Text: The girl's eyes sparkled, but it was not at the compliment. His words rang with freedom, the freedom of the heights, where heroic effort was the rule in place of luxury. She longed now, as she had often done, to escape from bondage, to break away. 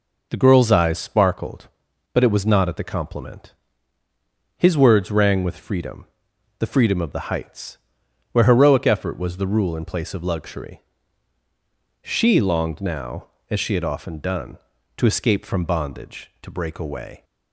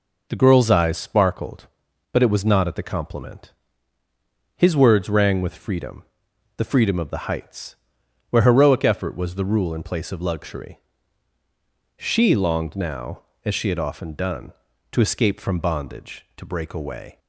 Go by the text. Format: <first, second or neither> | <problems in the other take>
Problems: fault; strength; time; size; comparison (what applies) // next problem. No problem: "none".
neither | none